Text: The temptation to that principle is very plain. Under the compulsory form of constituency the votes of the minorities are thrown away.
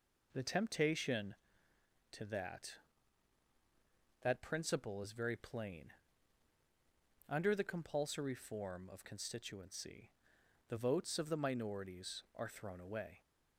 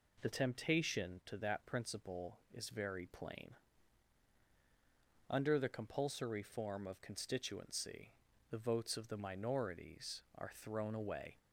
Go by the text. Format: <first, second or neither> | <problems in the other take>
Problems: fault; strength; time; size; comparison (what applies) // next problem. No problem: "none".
second | says "that" twice; at 4.2 s // pauses between "constituency" and "the"; noticeable; at 10.1 s; 0.58 s long; also in the second